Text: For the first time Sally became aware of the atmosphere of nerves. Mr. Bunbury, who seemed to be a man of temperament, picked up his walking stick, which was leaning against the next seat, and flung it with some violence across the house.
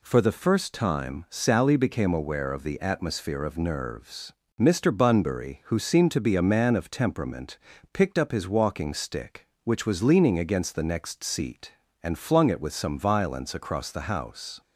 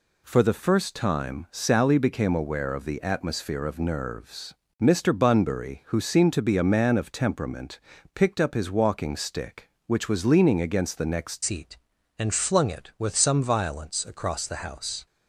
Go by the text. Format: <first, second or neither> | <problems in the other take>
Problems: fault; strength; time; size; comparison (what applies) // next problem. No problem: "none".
first | changes voice at "seat"; from 11.4 s on; 3.6 s long